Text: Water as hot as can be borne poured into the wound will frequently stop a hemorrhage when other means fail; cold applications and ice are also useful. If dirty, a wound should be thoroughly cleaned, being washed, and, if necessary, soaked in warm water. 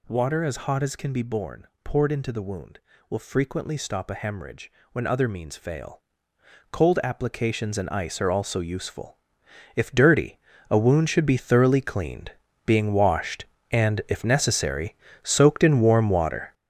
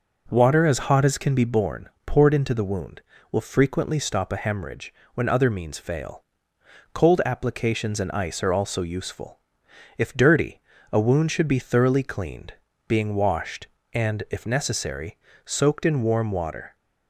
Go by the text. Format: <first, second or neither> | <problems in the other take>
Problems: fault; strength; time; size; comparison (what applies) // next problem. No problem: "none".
second | gets louder; strong; throughout; 9.5 dB // pauses between "borne" and "poured"; slight; at 1.6 s; 0.18 s long; slight in the second // pauses between "hemorrhage" and "when"; slight; at 4.7 s; 0.20 s long; slight in the second